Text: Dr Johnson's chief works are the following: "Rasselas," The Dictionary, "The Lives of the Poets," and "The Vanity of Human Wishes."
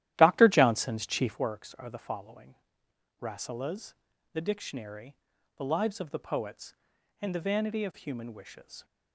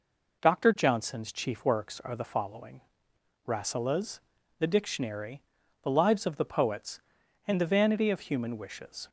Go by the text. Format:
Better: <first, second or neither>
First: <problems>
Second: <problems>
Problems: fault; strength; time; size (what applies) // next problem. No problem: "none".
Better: second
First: starts louder than the rest; strong; until 1.4 s; 13 dB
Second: none